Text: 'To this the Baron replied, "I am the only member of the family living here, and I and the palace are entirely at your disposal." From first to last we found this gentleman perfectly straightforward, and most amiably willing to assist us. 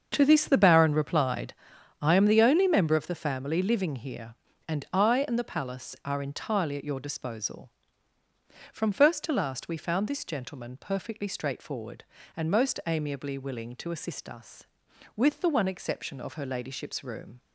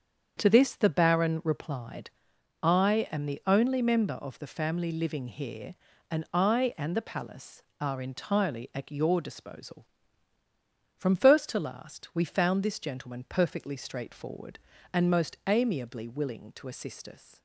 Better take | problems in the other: second | starts louder than the rest; until 1.1 s; 6.5 dB; strong in the second // goes on to say "With the one exception of her ladyship's room"; strong; from 15.1 s on; 2.2 s long

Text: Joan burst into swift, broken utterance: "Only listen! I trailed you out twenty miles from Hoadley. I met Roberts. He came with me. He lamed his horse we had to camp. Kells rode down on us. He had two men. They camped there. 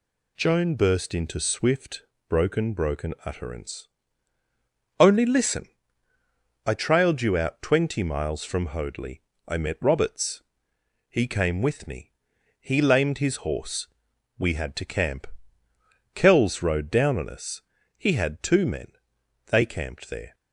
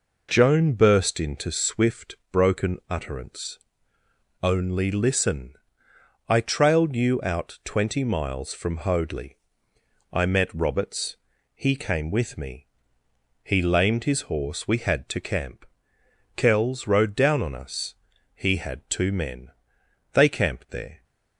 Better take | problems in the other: second | says "broken" twice; at 2.7 s // pauses between "horse" and "we"; noticeable; at 13.8 s; 0.50 s long

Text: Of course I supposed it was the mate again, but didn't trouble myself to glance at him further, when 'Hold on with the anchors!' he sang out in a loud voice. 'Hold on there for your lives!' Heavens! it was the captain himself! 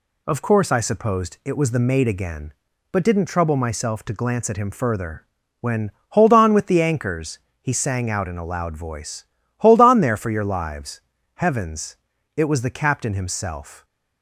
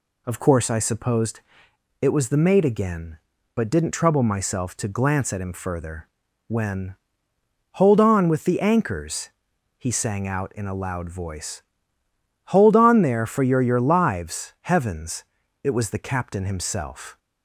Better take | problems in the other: first | pauses between "supposed" and "it"; noticeable; at 1.4 s; 0.60 s long // pauses between "when" and "Hold"; noticeable; at 6.9 s; 0.76 s long; slight in the first // says "your" twice; at 13.6 s

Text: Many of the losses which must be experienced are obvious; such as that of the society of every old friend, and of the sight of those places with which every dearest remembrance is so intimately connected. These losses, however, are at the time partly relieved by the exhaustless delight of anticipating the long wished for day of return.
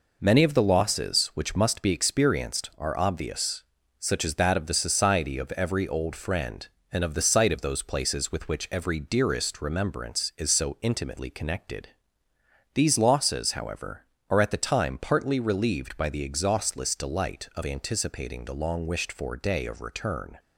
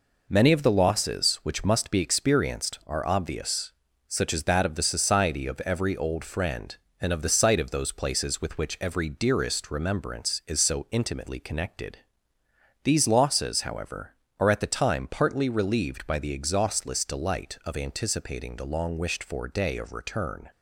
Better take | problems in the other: neither | none

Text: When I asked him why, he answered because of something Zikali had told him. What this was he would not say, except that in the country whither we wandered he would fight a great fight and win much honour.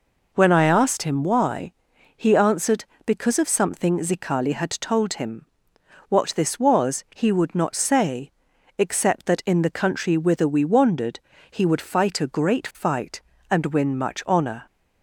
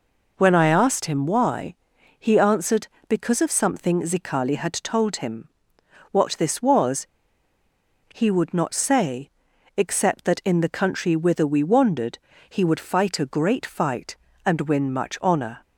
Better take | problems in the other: first | pauses between "was" and "he"; at 7.0 s; 1.0 s long // pauses between "wandered" and "he"; slight; at 12.1 s; 0.32 s long; slight in the first

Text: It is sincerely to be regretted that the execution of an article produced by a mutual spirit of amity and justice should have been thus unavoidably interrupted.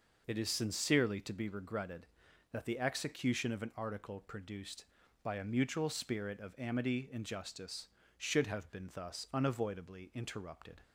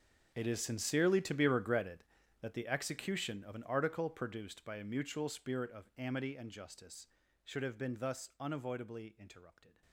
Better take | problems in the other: first | gets quieter; strong; throughout; 17.5 dB

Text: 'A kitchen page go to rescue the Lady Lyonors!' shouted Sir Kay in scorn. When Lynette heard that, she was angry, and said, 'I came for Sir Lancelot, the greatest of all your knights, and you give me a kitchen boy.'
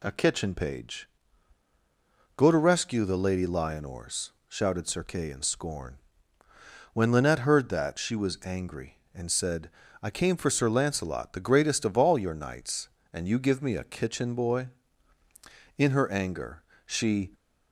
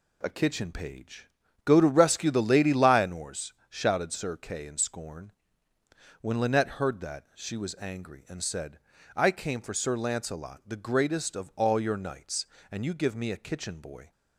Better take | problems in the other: second | pauses between "page" and "go"; strong; at 1.0 s; 1.2 s long; also in the second // goes on to say "In her anger she"; from 15.7 s on; 1.5 s long

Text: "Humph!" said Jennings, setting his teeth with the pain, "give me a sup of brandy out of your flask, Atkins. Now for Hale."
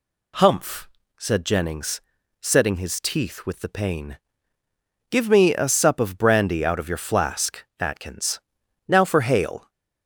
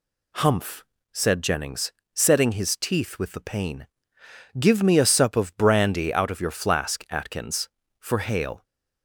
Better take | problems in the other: first | skips "Now"; at 7.8 s

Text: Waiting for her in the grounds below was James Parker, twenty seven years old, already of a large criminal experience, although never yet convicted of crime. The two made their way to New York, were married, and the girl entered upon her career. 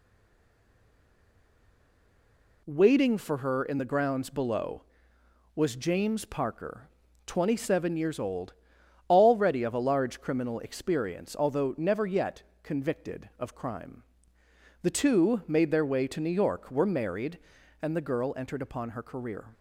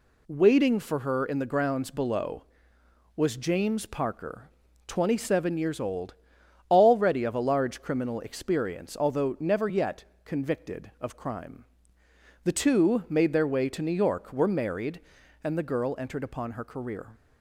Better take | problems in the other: second | stays silent before the first word; strong; until 2.6 s; 2.6 s long // pauses between "yet" and "convicted"; slight; at 12.4 s; 0.20 s long; slight in the second

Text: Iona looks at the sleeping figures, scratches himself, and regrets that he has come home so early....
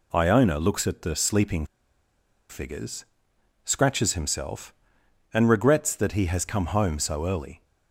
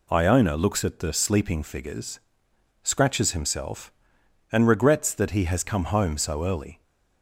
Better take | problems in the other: second | pauses between "sleeping" and "figures"; noticeable; at 1.6 s; 0.84 s long

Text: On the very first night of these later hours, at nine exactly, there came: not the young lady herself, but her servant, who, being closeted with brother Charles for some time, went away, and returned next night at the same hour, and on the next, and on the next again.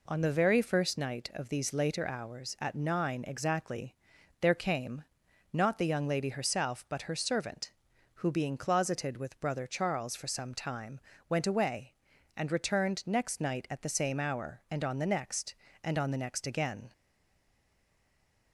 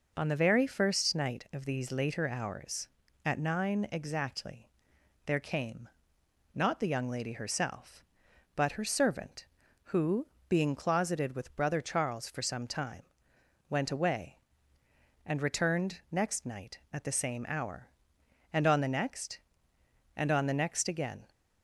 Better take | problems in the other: second | stays silent after the last word; noticeable; from 16.9 s on; 1.6 s long

